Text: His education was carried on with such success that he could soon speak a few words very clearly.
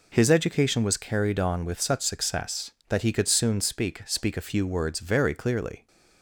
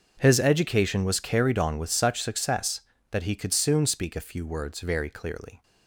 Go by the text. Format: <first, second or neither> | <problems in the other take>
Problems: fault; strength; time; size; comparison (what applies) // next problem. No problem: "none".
second | says "speak" twice; at 4.0 s